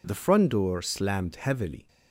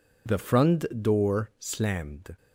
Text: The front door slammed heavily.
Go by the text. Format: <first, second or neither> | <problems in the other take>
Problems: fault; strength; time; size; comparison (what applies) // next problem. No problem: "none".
first | pauses between "front" and "door"; slight; at 0.8 s; 0.18 s long // stops before "heavily"; at 2.3 s